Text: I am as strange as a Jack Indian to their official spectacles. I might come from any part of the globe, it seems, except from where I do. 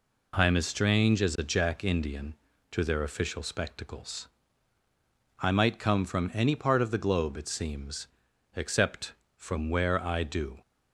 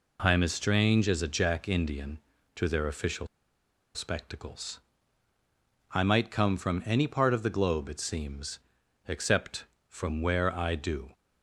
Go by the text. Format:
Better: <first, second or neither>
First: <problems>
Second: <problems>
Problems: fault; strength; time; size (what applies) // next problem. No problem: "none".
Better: first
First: none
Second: pauses between "official" and "spectacles"; noticeable; at 3.2 s; 0.68 s long